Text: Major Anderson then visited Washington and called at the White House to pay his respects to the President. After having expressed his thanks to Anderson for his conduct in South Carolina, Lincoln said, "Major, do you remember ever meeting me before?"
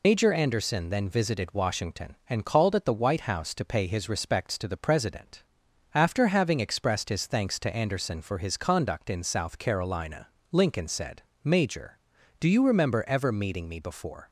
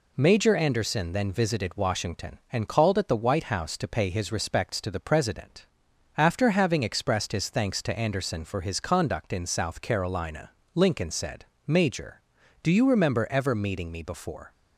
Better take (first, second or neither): second